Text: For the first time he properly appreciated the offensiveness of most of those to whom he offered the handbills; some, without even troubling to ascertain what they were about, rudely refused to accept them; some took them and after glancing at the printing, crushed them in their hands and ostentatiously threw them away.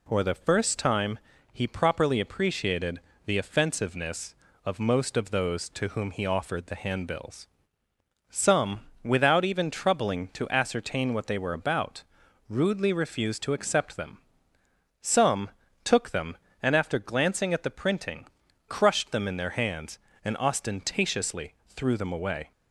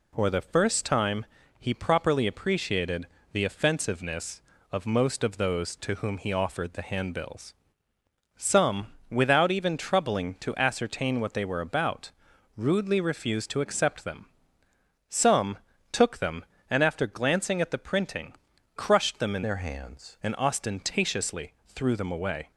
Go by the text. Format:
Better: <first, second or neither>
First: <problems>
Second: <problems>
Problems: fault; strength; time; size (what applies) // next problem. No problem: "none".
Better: first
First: pauses between "time" and "he"; slight; at 1.1 s; 0.32 s long // pauses between "appreciated" and "the"; slight; at 3.0 s; 0.24 s long // pauses between "some" and "took"; slight; at 15.4 s; 0.32 s long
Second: pauses between "time" and "he"; slight; at 1.2 s; 0.32 s long // pauses between "appreciated" and "the"; slight; at 3.0 s; 0.24 s long // pauses between "some" and "took"; slight; at 15.5 s; 0.32 s long // changes voice from "their" to "hands"; from 19.4 to 20.1 s; 0.7 s long